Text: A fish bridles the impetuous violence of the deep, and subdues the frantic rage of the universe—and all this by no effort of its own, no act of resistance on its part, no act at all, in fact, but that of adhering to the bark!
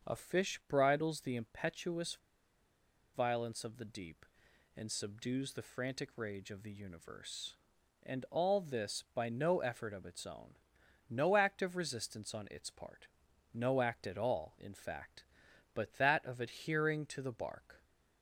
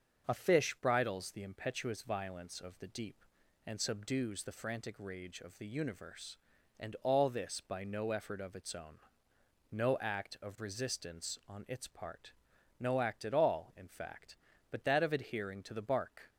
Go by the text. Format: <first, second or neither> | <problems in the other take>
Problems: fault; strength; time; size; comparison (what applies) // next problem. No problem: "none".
second | starts louder than the rest; until 1.1 s; 6.5 dB; also in the second // pauses between "impetuous" and "violence"; at 2.1 s; 0.98 s long